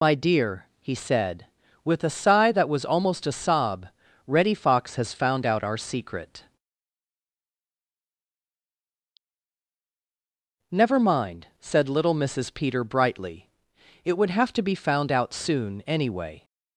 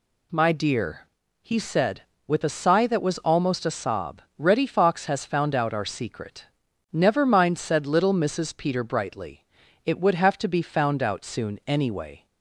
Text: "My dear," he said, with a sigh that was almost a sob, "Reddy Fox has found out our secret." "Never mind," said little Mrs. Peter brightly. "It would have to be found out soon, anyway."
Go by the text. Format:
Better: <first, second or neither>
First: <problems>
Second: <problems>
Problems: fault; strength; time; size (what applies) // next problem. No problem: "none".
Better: second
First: loses the start of "My"; at 0.0 s; 70 ms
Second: none